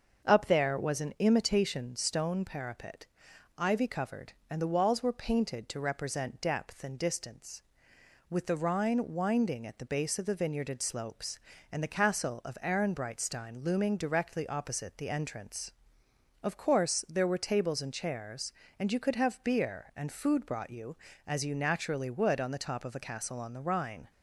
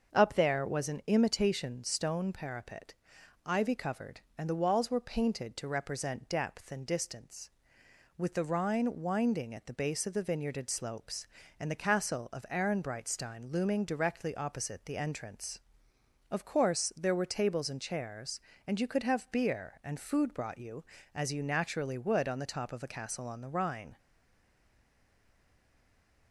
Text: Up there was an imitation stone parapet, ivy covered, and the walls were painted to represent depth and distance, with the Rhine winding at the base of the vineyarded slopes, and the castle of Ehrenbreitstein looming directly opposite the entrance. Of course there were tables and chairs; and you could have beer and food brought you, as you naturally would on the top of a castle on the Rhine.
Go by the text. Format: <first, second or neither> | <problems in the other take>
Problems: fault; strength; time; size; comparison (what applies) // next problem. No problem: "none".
first | starts louder than the rest; until 1.1 s; 6.5 dB; also in the first // stays silent after the last word; from 23.9 s on; 2.4 s long